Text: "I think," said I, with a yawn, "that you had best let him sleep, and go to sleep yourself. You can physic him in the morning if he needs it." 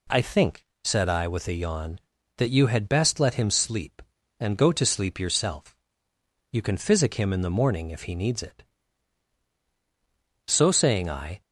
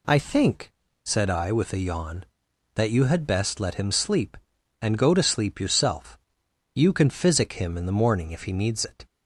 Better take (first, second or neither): second